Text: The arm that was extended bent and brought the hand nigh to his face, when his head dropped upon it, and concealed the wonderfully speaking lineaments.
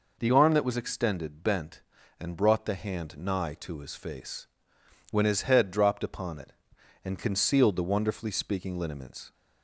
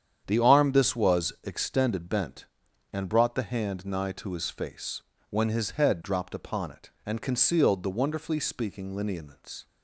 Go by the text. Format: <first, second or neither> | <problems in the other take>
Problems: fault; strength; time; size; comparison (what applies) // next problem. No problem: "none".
first | starts louder than the rest; strong; until 1.2 s; 8.5 dB // says "this" for "that"; at 0.7 s